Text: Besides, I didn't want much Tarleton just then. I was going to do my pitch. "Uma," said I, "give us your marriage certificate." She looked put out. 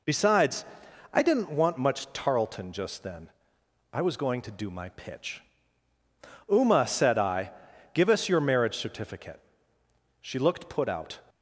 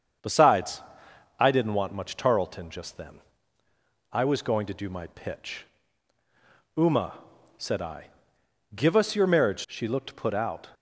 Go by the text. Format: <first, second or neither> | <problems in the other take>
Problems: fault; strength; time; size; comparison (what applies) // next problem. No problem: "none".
first | starts louder than the rest; strong; until 1.7 s; 7 dB // skips "certificate"; at 9.6 s